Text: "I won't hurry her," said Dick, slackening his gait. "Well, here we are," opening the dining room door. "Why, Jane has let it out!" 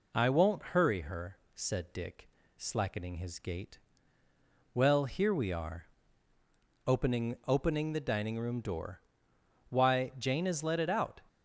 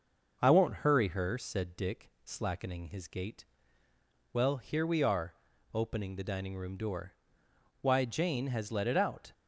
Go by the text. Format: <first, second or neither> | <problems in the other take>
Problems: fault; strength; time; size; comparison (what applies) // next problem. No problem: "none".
second | says "opening" twice; at 7.4 s